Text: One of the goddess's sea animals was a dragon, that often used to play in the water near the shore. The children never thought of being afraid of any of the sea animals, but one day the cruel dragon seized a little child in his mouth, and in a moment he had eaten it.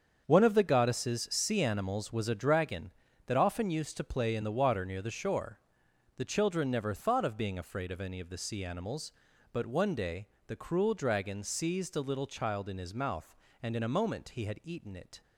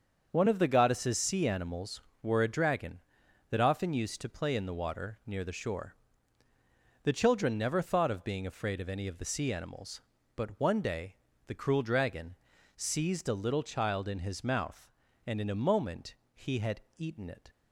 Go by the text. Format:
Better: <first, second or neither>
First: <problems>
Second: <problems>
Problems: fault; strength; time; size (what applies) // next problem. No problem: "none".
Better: first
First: starts louder than the rest; strong; until 1.2 s; 7 dB // pauses between "day" and "the"; slight; at 10.2 s; 0.18 s long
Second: starts louder than the rest; until 1.3 s; 6.5 dB // says "were" for "was"; at 2.2 s // pauses between "day" and "the"; slight; at 11.1 s; 0.32 s long // pauses between "dragon" and "seized"; at 12.3 s; 0.40 s long // pauses between "moment" and "he"; slight; at 16.1 s; 0.22 s long // pauses between "had" and "eaten"; slight; at 16.7 s; 0.16 s long